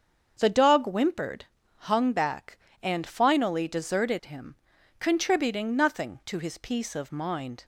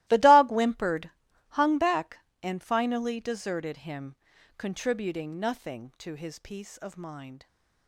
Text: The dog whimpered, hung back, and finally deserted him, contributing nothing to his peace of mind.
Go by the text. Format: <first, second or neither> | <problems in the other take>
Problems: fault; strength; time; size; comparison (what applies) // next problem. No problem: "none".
first | gets quieter; strong; throughout; 17.5 dB // starts louder than the rest; strong; until 1.0 s; 17 dB; also in the first